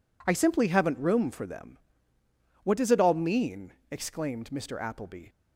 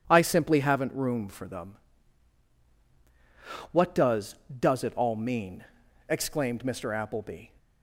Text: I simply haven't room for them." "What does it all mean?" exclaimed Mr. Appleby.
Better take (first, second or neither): first